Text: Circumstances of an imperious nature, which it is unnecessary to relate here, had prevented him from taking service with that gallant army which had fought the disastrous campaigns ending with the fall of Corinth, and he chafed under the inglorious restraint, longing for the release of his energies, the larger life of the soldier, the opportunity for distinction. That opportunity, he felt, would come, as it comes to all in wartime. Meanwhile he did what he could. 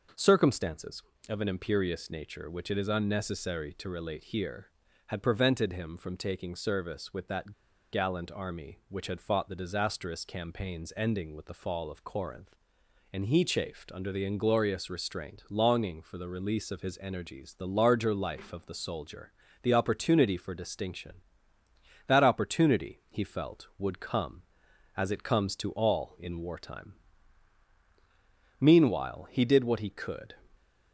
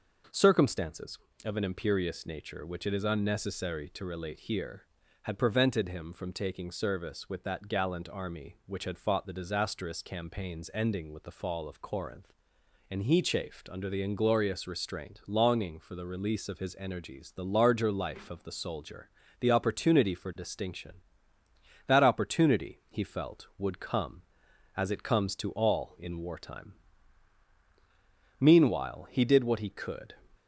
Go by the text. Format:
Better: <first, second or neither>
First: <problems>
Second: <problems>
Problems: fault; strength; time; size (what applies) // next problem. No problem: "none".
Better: second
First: pauses between "that" and "gallant"; at 7.5 s; 0.41 s long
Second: none